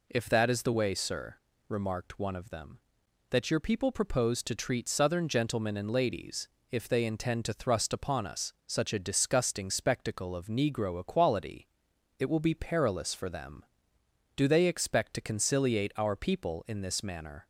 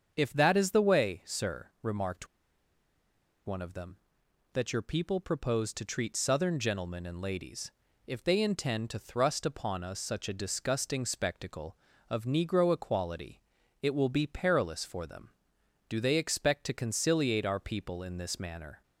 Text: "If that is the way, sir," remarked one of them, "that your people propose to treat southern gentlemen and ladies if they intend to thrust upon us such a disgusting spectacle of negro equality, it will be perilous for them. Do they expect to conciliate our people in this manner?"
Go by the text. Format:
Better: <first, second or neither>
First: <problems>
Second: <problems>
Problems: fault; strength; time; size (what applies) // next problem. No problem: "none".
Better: first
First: pauses between "ladies" and "if"; slight; at 6.4 s; 0.22 s long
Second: starts louder than the rest; strong; until 1.1 s; 7 dB // pauses between "remarked" and "one"; at 2.2 s; 1.1 s long // pauses between "ladies" and "if"; slight; at 7.7 s; 0.34 s long